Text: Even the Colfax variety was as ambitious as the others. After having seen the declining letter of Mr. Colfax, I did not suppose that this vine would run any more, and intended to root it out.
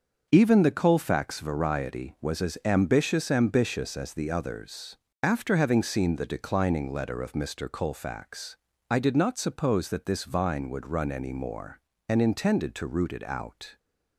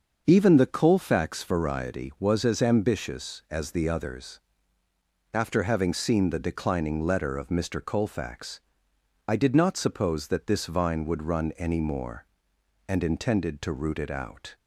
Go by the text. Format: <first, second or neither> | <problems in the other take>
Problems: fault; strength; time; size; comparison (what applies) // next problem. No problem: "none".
second | starts louder than the rest; until 1.3 s; 6.5 dB; also in the second // says "ambitious" twice; at 3.2 s